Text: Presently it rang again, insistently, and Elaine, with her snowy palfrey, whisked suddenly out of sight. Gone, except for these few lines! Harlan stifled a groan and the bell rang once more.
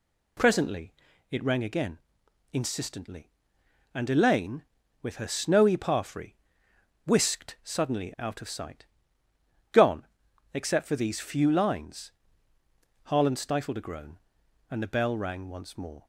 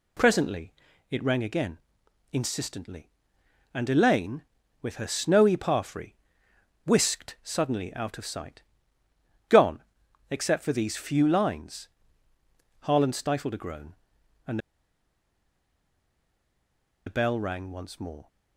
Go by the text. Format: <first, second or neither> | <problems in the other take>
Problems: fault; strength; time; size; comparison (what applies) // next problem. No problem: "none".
first | pauses between "Presently" and "it"; at 0.7 s; 0.40 s long; also in the first // pauses between "and" and "the"; strong; at 14.5 s; 2.4 s long